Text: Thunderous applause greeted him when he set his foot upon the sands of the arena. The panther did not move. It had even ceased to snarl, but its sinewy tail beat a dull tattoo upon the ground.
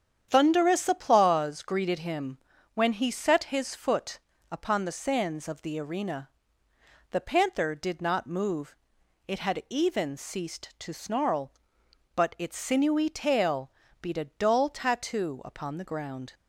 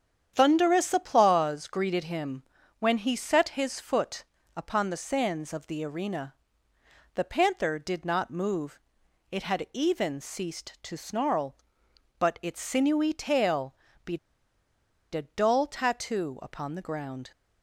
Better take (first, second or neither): first